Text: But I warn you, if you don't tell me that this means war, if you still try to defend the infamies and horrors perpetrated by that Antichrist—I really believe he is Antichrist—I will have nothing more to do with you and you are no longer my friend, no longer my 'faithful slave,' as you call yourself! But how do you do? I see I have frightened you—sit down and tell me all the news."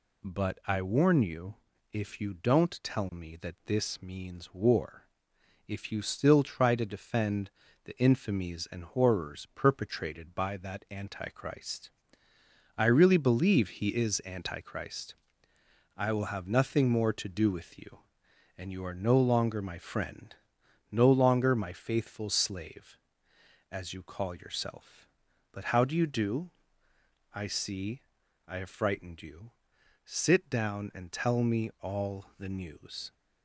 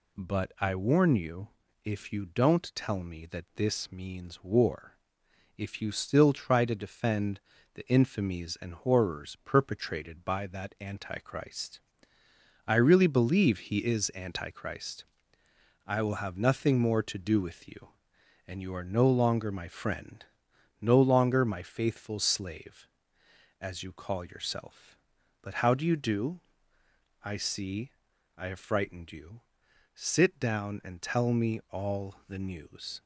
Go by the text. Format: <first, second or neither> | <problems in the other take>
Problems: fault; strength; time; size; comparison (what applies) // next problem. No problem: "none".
neither | pauses between "defend" and "the"; slight; the same in both // pauses between "see" and "I"; the same in both